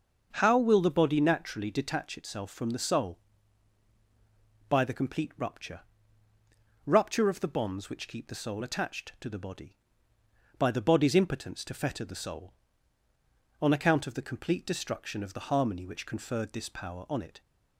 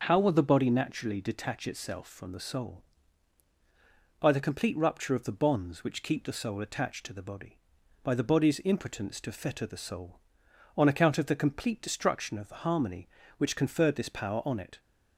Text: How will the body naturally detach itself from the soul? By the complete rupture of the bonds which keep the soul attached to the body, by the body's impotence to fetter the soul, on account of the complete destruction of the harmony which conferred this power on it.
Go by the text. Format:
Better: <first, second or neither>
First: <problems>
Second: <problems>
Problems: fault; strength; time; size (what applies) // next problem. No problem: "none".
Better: second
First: starts louder than the rest; until 1.3 s; 6.5 dB // says "rupture" twice; at 6.8 s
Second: starts louder than the rest; noticeable; until 1.0 s; 6 dB